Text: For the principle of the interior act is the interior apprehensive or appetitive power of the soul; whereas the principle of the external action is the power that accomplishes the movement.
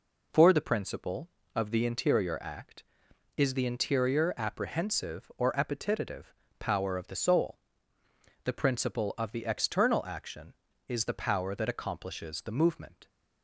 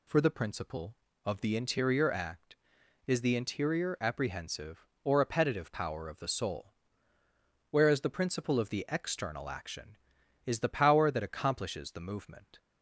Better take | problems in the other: second | pauses between "appetitive" and "power"; slight; at 6.3 s; 0.28 s long // skips "whereas"; at 8.0 s

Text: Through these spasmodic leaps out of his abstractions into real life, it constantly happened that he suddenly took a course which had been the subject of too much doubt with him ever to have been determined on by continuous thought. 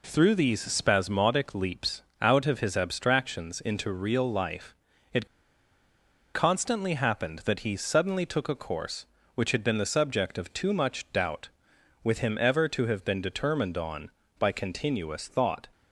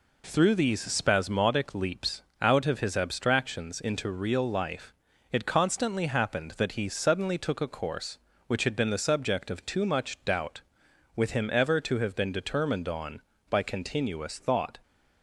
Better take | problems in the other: second | pauses between "leaps" and "out"; slight; at 2.0 s; 0.18 s long; slight in the second // pauses between "it" and "constantly"; at 5.2 s; 1.0 s long

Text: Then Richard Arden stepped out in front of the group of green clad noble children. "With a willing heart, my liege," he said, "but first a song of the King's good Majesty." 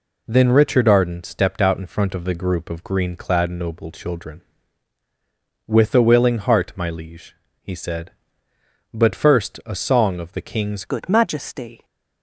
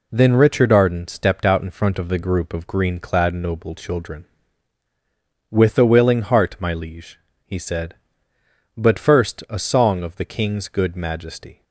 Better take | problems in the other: second | changes voice at "good"; from 10.8 s on; 1.0 s long

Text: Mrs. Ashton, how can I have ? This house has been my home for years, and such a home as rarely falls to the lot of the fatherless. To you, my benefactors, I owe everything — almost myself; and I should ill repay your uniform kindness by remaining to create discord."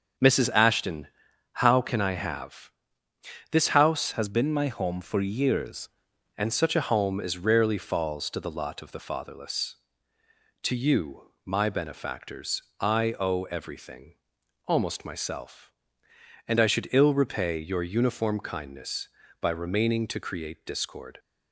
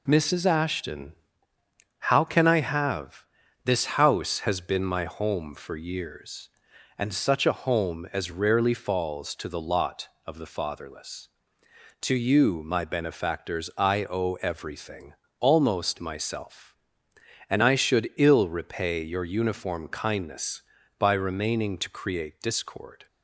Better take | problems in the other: second | starts louder than the rest; until 1.6 s; 7 dB // changes voice from "has" to "years"; from 4.1 to 5.8 s; 1.7 s long

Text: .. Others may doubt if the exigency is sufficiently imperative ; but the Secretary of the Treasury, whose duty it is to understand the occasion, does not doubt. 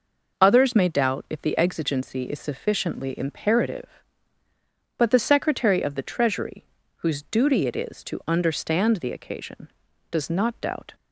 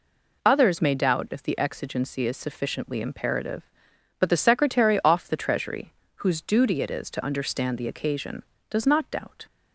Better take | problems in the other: first | says "off" for "of"; at 5.0 s

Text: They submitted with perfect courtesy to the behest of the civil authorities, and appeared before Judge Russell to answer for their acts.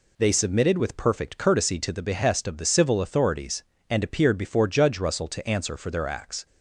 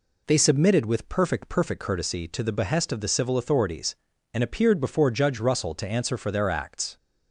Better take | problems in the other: first | says "perfect" twice; at 1.4 s

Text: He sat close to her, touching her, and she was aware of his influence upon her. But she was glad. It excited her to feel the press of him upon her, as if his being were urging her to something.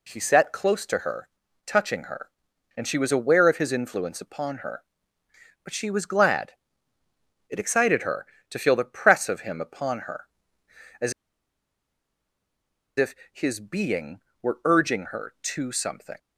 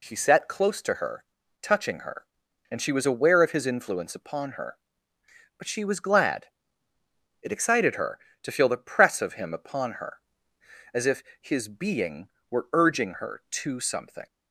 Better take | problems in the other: second | pauses between "as" and "if"; strong; at 11.1 s; 1.8 s long // pauses between "if" and "his"; slight; at 13.1 s; 0.18 s long; slight in the second

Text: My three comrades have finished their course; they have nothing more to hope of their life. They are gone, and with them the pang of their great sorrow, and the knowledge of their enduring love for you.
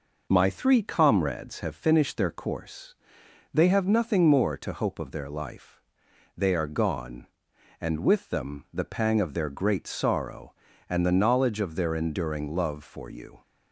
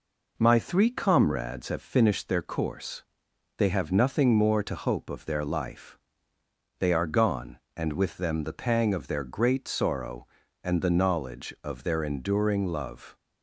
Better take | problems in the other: first | stops before "for you"; at 13.1 s

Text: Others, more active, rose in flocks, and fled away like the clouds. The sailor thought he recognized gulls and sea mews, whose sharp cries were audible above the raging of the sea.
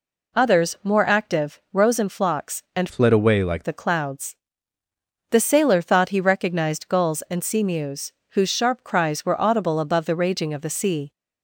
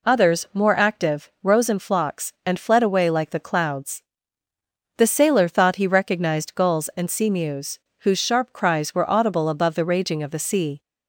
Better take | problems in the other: second | changes voice from "fled" to "like"; from 2.8 to 3.6 s; 0.8 s long

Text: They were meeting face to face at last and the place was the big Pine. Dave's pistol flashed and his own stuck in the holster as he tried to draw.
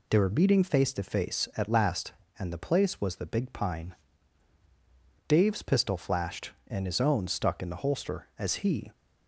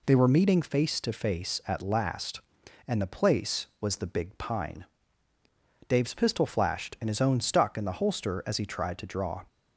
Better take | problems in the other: second | stops before "tried to draw"; at 8.9 s

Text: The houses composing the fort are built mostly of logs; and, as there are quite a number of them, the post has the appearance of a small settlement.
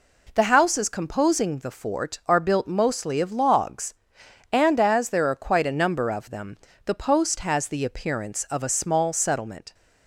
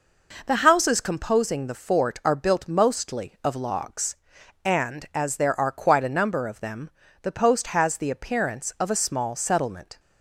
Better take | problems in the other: neither | none

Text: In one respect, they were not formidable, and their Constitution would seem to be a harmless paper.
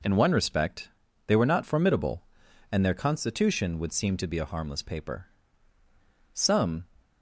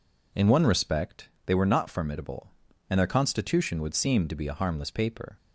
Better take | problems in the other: second | goes on to say "Some"; from 6.3 s on; 0.52 s long

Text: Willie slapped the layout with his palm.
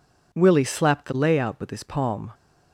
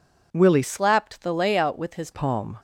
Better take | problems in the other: first | changes voice from "slapped" to "his"; from 0.6 to 2.0 s; 1.4 s long

